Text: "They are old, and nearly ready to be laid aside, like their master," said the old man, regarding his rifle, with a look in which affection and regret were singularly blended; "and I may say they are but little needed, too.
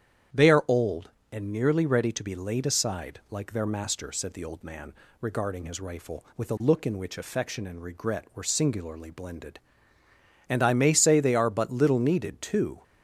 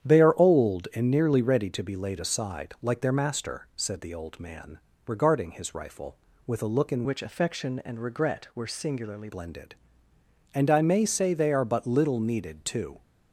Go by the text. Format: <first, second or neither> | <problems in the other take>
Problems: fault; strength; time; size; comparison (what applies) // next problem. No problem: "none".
first | starts louder than the rest; strong; until 1.1 s; 9.5 dB; strong in the first // changes voice from "which" to "singularly"; from 7.0 to 9.2 s; 2.2 s long